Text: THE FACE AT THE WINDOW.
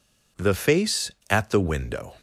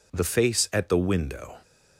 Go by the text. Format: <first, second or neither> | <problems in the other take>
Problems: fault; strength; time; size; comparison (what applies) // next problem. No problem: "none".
neither | none